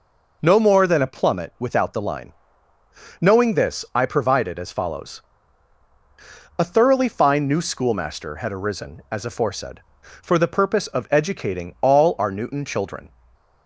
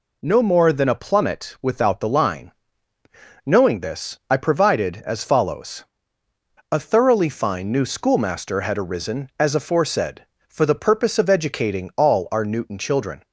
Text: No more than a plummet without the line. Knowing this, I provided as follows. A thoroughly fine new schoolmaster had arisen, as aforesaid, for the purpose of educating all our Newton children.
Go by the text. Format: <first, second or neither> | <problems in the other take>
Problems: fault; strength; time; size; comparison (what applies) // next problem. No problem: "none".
neither | none